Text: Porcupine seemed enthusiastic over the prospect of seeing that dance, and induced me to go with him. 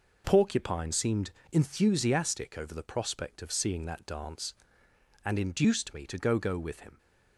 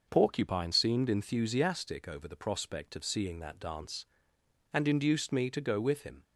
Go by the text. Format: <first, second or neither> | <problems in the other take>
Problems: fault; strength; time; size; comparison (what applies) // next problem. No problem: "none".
second | pauses between "seemed" and "enthusiastic"; slight; at 1.2 s; 0.22 s long // says "go" twice; at 6.3 s